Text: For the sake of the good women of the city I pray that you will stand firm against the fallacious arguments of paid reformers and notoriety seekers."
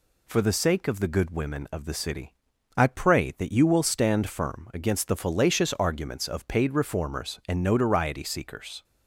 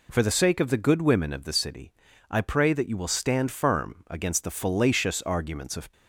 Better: first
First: pauses between "city" and "I"; at 2.3 s; 0.42 s long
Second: pauses between "city" and "I"; at 1.9 s; 0.40 s long // stops before "paid reformers and notoriety seekers"; at 5.9 s

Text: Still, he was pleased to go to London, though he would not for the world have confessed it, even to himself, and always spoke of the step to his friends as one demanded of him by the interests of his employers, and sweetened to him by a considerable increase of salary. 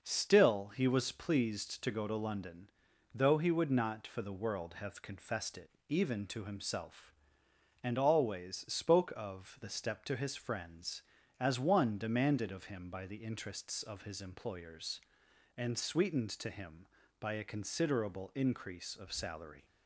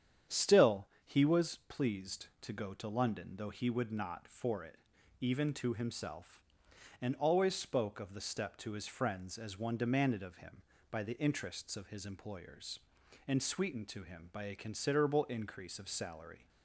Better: first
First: none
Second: starts louder than the rest; strong; until 1.4 s; 9 dB // skips "the world have confessed"; at 4.6 s

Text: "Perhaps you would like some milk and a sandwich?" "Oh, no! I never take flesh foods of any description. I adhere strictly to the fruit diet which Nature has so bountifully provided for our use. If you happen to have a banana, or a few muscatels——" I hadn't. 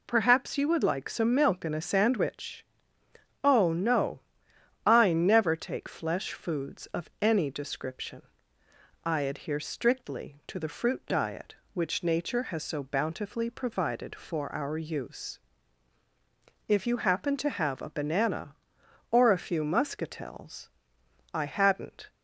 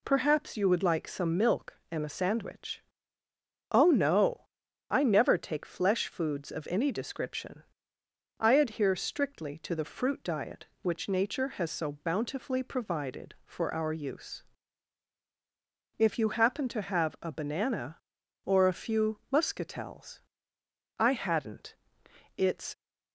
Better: first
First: none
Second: goes on to say "It's"; slight; from 22.3 s on; 0.38 s long

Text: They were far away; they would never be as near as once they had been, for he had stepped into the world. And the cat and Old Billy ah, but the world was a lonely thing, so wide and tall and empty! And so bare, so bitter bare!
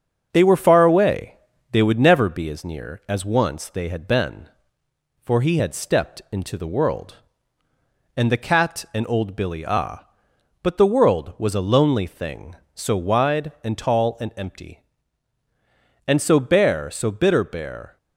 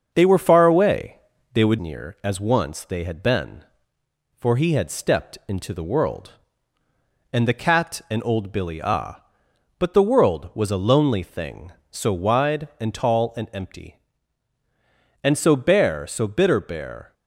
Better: first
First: starts louder than the rest; until 1.3 s; 6.5 dB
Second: starts louder than the rest; until 1.1 s; 6.5 dB // skips "never be as"; at 1.7 s

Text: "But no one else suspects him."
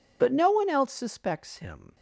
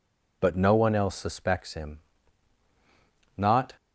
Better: first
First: none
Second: goes on to say "Not"; slight; from 3.3 s on; 0.34 s long

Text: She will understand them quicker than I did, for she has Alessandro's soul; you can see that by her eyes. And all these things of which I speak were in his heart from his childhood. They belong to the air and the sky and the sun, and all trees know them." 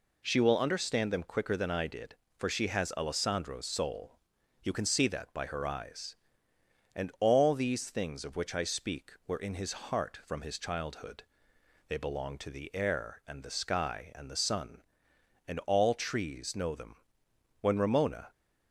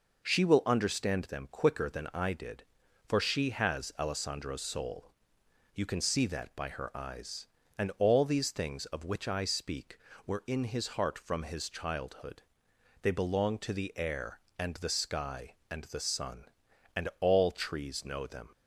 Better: second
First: goes on to say "When Ramona"; noticeable; from 17.5 s on; 0.70 s long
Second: none

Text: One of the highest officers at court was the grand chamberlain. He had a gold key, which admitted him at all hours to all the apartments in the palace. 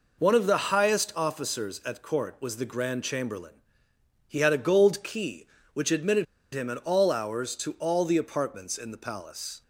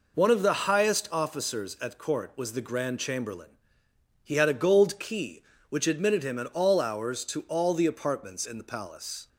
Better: second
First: pauses between "admitted" and "him"; slight; at 6.2 s; 0.28 s long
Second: none

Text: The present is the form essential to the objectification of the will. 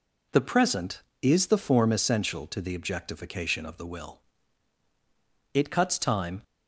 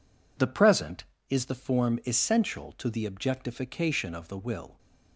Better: second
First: goes on to say "It cuts time"; noticeable; from 5.5 s on; 0.88 s long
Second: none

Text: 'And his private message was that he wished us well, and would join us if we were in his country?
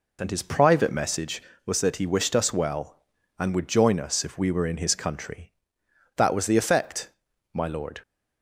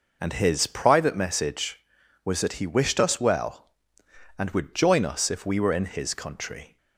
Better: second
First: goes on to say "That was the effect my lord"; strong; from 6.1 s on; 1.8 s long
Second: none

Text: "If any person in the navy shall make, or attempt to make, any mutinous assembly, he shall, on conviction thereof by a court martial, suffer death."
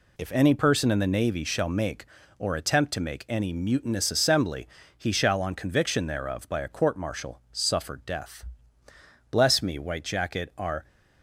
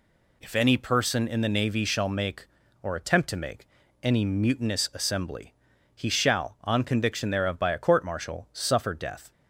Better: second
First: goes on to say "Bless me White Jacket are"; from 9.2 s on; 1.5 s long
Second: none

